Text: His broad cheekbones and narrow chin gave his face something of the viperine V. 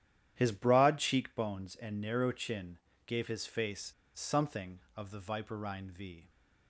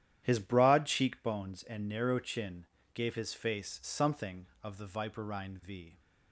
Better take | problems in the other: second | starts louder than the rest; strong; until 1.3 s; 11 dB; strong in the second // pauses between "chin" and "gave"; slight; at 2.7 s; 0.30 s long; slight in the second // pauses between "face" and "something"; slight; at 3.9 s; 0.24 s long

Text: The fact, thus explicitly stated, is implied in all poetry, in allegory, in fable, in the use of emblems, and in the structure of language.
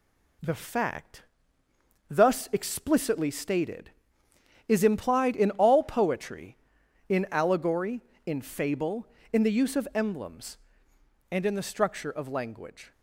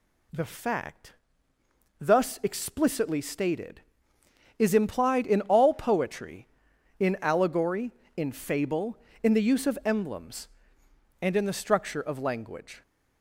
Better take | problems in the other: second | gets quieter; slight; throughout; 2.5 dB

